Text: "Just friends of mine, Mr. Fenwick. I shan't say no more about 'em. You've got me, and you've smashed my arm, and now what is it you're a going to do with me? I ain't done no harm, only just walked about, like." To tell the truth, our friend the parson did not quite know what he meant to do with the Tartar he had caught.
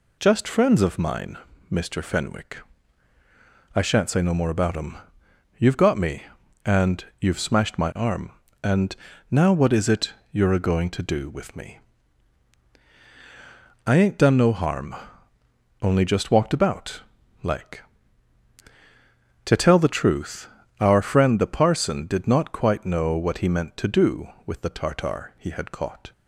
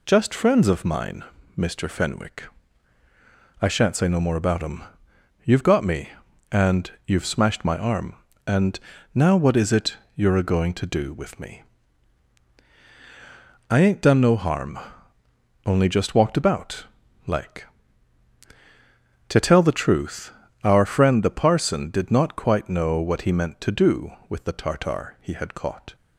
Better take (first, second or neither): neither